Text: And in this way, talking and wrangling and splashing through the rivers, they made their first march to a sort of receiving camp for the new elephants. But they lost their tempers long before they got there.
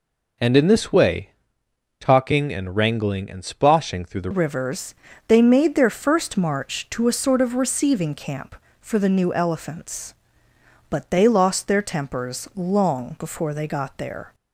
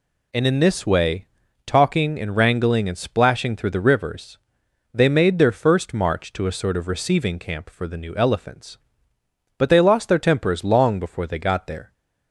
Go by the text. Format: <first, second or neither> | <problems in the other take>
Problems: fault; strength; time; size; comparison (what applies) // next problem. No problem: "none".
second | changes voice at "rivers"; from 4.3 s on; 10.0 s long